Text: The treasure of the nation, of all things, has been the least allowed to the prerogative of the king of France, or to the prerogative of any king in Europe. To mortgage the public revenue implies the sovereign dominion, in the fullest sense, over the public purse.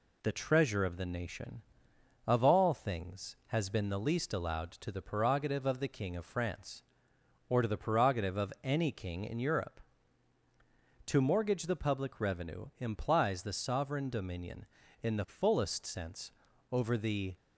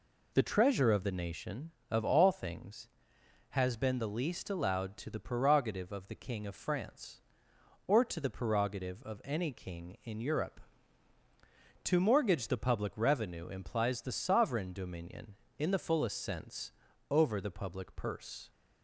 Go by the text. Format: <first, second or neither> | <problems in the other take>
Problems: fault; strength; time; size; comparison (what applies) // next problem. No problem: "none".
second | stops before "public purse"; at 17.3 s